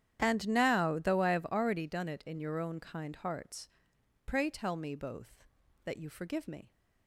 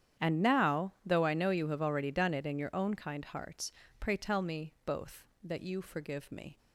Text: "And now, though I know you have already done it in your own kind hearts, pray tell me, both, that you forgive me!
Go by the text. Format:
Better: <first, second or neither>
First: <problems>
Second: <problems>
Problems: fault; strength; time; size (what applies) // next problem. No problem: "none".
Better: second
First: starts louder than the rest; strong; until 1.2 s; 10 dB // skips "know you"; at 1.3 s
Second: starts louder than the rest; strong; until 1.3 s; 9.5 dB